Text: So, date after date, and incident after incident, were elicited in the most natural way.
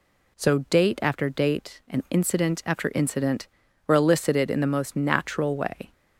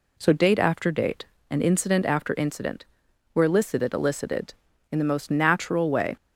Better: first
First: none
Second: says "elicited" twice; at 3.9 s

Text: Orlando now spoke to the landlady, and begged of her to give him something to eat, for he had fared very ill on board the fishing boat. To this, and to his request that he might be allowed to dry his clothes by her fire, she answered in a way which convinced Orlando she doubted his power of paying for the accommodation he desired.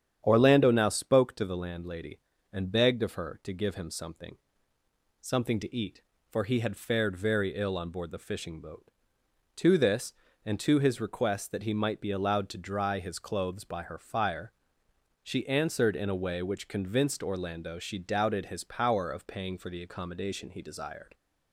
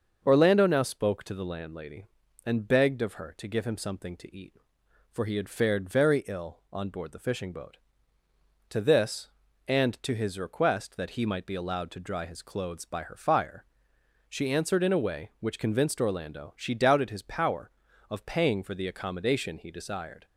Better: second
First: starts louder than the rest; strong; until 1.2 s; 9 dB // says "something" twice; at 5.1 s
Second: starts louder than the rest; noticeable; until 1.2 s; 6 dB

